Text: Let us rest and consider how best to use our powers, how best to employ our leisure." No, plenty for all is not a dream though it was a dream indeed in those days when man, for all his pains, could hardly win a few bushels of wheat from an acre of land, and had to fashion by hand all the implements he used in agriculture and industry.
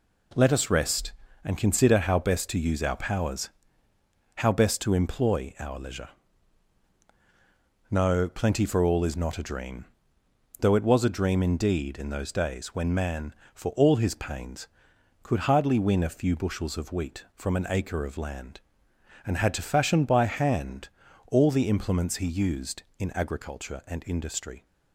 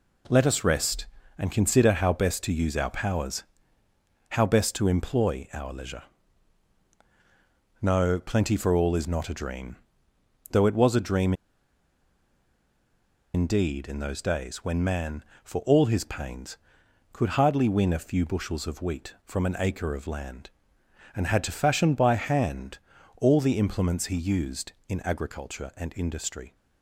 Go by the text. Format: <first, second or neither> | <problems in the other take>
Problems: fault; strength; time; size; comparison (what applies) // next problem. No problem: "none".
first | pauses between "dream" and "though"; noticeable; at 9.7 s; 0.76 s long; noticeable in the first // pauses between "dream" and "indeed"; strong; at 11.3 s; 2.0 s long // pauses between "hand" and "all"; at 22.7 s; 0.40 s long; also in the first